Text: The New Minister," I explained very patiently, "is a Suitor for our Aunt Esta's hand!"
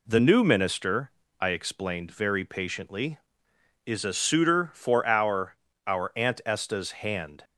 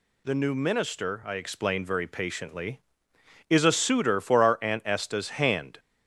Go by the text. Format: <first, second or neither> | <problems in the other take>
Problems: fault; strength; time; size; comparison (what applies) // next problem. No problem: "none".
second | says "our" twice; at 5.8 s